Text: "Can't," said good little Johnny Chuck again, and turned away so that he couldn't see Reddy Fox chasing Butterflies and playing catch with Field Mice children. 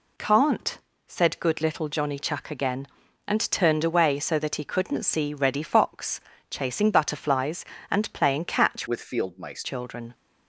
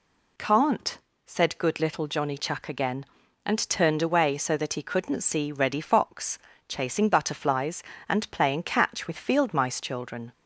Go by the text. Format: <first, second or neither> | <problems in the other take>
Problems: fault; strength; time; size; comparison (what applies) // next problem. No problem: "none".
second | pauses between "Fox" and "chasing"; slight; at 6.2 s; 0.28 s long; slight in the second // changes voice from "with" to "Mice"; from 8.8 to 9.6 s; 0.8 s long